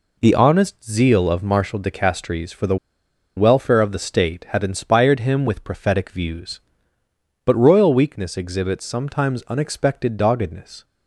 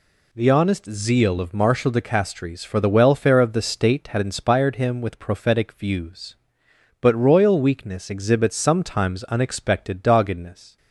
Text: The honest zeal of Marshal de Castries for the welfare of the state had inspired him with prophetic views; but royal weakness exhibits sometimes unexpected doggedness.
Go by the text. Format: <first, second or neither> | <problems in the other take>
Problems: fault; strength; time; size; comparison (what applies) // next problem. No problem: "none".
second | pauses between "the" and "welfare"; noticeable; at 2.7 s; 0.61 s long